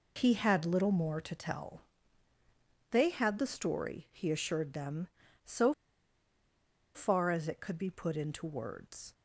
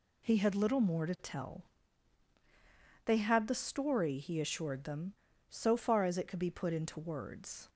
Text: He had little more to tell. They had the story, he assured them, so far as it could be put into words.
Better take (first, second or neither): second